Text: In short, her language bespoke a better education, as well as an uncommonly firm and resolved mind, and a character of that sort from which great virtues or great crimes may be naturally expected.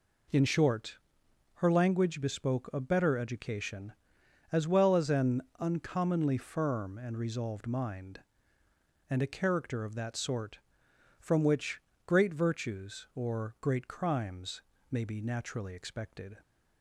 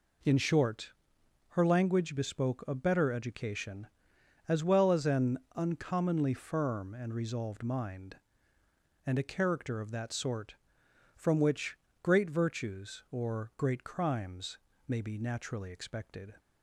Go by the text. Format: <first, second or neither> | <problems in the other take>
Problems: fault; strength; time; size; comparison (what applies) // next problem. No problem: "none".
neither | pauses between "an" and "uncommonly"; slight; the same in both // pauses between "which" and "great"; slight; the same in both // pauses between "crimes" and "may"; slight; the same in both